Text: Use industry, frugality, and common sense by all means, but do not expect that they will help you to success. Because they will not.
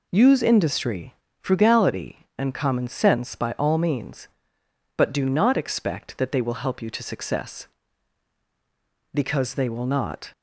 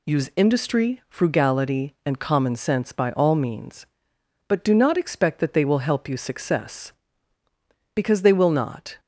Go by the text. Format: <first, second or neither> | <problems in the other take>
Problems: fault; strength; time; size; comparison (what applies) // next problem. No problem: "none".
first | skips "to"; at 6.1 s